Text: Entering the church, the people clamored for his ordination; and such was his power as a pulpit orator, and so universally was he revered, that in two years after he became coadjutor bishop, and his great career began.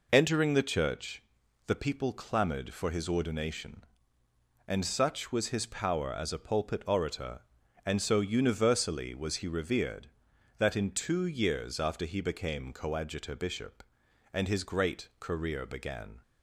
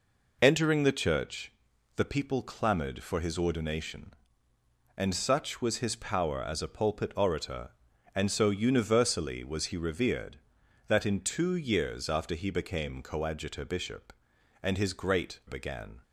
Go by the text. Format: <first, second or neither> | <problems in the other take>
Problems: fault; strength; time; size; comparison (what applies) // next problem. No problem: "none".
first | skips "career"; at 15.4 s